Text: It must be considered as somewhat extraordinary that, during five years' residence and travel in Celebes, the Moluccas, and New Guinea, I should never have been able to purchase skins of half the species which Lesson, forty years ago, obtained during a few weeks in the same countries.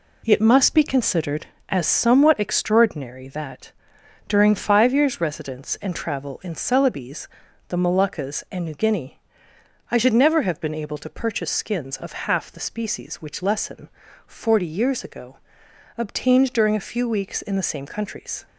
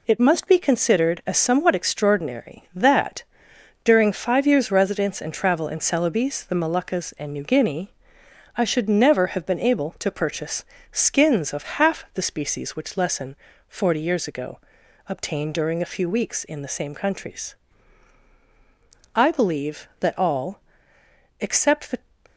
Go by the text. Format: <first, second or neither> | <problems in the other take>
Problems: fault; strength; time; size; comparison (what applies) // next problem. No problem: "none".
first | pauses between "purchase" and "skins"; slight; at 10.6 s; 0.26 s long // goes on to say "I believe that all except the"; strong; from 19.1 s on; 2.8 s long